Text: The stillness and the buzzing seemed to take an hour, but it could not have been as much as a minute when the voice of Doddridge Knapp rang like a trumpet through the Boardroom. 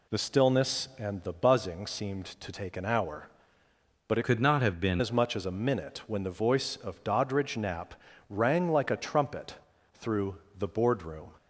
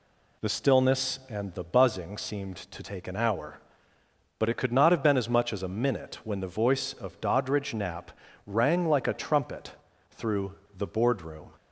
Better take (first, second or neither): second